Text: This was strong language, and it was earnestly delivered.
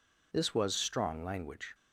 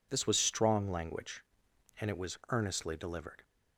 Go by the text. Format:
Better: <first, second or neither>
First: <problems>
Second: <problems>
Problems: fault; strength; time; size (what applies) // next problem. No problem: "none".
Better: second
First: stops before "and it was earnestly delivered"; at 1.7 s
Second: none